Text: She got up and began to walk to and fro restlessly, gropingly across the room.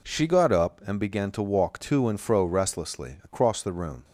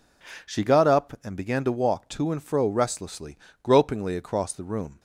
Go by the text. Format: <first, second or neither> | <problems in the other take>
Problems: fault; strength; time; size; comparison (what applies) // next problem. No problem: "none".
second | skips "gropingly"; at 3.1 s